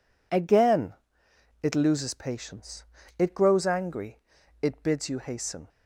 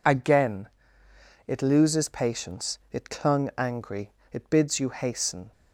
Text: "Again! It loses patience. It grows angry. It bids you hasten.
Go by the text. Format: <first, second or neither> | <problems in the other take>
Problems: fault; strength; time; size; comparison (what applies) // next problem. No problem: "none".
first | says "clung" for "grows"; at 3.0 s